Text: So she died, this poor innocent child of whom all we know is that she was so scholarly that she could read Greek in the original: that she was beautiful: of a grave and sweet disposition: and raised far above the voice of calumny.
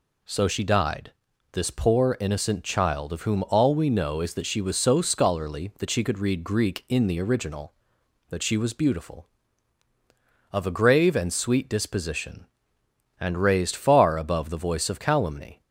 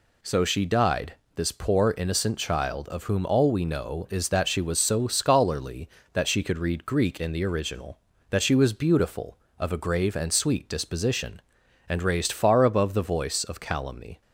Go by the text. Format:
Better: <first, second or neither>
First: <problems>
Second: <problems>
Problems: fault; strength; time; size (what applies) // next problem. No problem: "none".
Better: neither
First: none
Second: none